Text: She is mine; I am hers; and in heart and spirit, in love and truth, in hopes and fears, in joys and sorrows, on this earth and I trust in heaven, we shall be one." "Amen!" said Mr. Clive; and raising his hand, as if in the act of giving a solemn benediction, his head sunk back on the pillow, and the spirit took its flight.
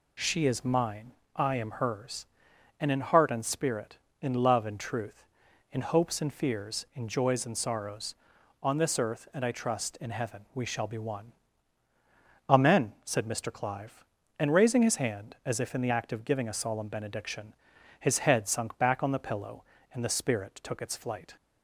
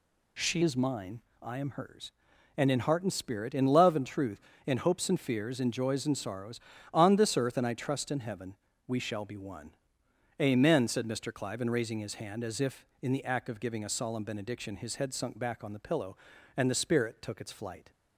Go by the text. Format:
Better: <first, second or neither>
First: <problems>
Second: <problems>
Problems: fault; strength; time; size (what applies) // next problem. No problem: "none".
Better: first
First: none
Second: changes voice at "is"; from 0.6 s on; 17.3 s long